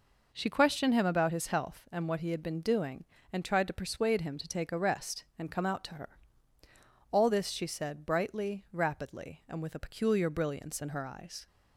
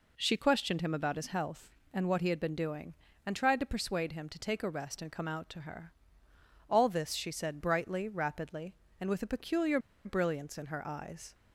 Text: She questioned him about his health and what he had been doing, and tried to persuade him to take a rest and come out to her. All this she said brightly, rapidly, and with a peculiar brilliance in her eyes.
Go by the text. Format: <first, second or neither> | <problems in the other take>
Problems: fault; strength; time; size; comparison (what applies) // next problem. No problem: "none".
first | pauses between "peculiar" and "brilliance"; slight; at 9.7 s; 0.26 s long